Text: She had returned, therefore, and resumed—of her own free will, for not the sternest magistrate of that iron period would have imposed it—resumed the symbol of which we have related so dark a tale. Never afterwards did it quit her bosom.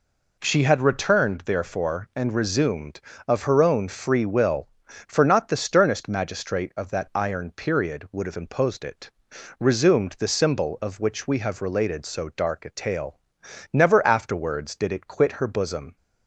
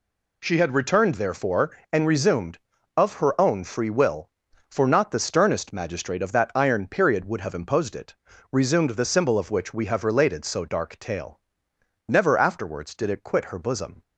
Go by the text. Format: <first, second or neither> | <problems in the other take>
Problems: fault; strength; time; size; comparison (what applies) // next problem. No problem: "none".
first | skips "a"; at 10.9 s